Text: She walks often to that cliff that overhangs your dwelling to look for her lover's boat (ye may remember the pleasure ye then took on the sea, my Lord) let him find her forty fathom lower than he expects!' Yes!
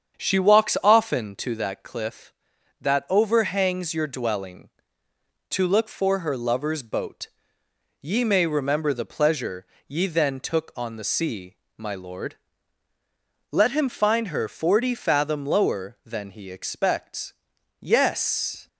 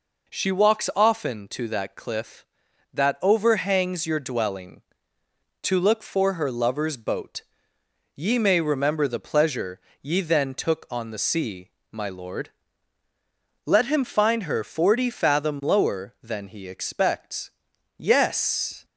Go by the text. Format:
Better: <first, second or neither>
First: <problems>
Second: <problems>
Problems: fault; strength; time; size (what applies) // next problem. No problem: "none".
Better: second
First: starts louder than the rest; strong; until 1.6 s; 7.5 dB // pauses between "pleasure" and "ye"; slight; at 9.6 s; 0.22 s long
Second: pauses between "pleasure" and "ye"; slight; at 9.7 s; 0.22 s long